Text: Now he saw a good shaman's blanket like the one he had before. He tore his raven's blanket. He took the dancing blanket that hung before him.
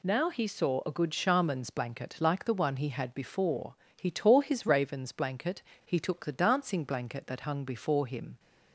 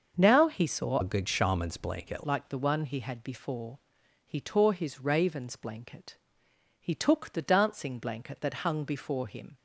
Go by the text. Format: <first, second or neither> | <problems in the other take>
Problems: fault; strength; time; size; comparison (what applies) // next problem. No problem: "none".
first | starts louder than the rest; until 1.1 s; 6.5 dB // changes voice from "a" to "blanket"; from 1.0 to 2.2 s; 1.2 s long